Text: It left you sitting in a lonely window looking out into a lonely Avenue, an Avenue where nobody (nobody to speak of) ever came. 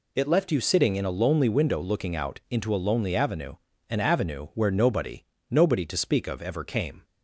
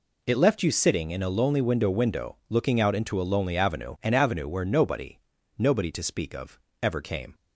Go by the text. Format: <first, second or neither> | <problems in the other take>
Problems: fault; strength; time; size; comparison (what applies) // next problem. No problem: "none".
first | says "window" twice; at 1.9 s